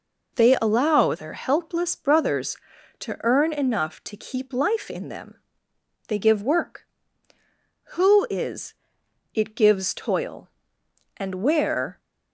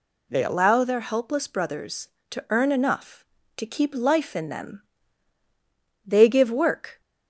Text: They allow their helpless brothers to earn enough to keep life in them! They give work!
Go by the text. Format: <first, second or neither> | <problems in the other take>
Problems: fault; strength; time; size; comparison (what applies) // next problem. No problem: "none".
second | goes on to say "Who is it gives toil and where"; strong; from 7.9 s on; 4.0 s long